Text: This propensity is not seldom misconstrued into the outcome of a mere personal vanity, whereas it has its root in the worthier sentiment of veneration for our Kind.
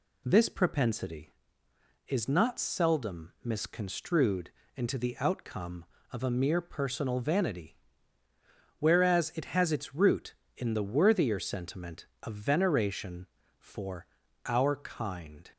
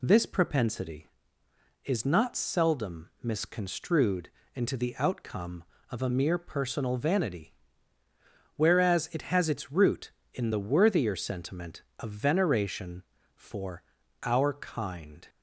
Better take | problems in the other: neither | pauses between "misconstrued" and "into"; slight; the same in both // pauses between "for" and "our"; the same in both

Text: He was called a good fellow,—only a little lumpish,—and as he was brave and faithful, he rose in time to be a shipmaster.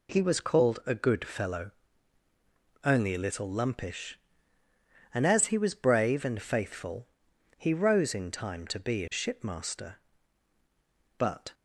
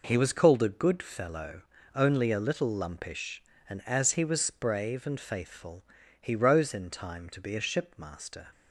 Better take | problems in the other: second | goes on to say "But"; slight; from 11.1 s on; 0.36 s long

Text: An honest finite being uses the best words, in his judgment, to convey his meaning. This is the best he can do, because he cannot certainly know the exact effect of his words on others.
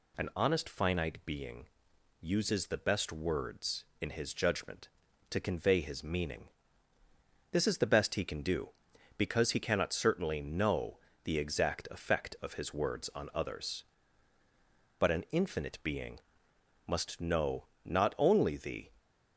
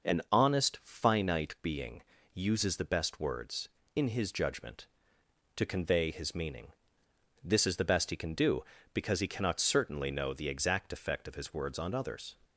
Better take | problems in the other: second | pauses between "being" and "uses"; noticeable; at 1.6 s; 0.56 s long; slight in the second // pauses between "know" and "the"; slight; at 10.9 s; 0.26 s long // goes on to say "But an infinite being must know not only the"; strong; from 14.9 s on; 3.9 s long

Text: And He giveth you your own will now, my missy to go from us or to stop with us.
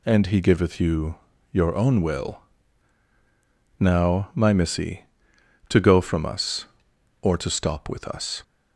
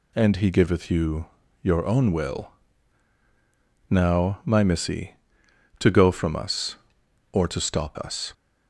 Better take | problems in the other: first | pauses between "you" and "your"; at 1.2 s; 0.38 s long; also in the first // pauses between "will" and "now"; strong; at 2.4 s; 1.4 s long; strong in the first // skips "with"; at 7.9 s

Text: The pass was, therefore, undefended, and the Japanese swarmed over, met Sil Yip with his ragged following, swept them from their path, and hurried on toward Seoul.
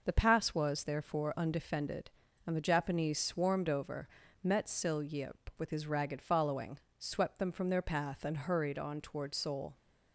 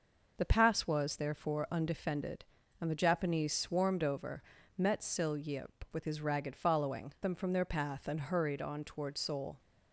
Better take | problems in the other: first | skips "swept"; at 7.1 s

